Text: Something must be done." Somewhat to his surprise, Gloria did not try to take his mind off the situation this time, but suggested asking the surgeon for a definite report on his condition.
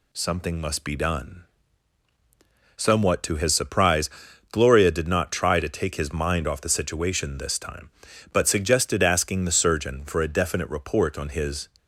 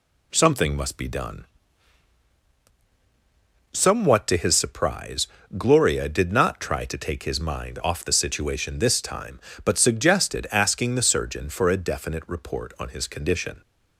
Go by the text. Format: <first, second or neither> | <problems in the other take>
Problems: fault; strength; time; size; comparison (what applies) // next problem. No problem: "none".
second | stops before "condition"; at 11.7 s